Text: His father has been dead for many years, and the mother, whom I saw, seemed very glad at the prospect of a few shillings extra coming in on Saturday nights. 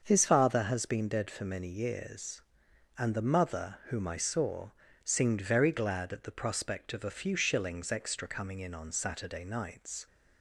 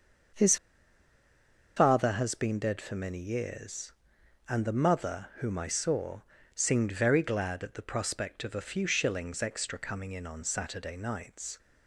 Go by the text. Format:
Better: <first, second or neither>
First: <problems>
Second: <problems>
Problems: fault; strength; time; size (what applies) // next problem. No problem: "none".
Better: first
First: starts louder than the rest; until 1.0 s; 6.5 dB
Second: starts louder than the rest; until 2.5 s; 6.5 dB // pauses between "His" and "father"; at 0.5 s; 1.2 s long